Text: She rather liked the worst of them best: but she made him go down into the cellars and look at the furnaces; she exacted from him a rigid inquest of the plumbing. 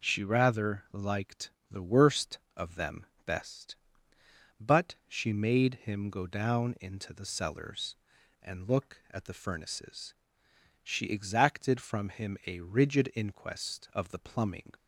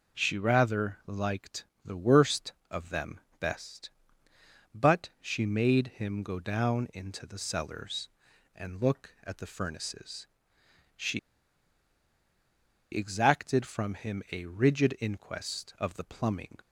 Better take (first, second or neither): first